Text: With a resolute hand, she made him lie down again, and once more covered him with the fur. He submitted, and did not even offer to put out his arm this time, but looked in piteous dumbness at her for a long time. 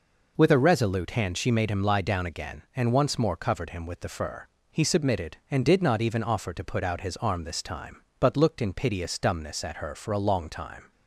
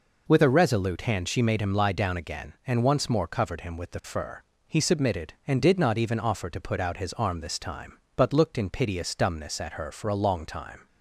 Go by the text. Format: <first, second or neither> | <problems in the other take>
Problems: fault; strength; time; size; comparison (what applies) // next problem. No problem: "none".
neither | none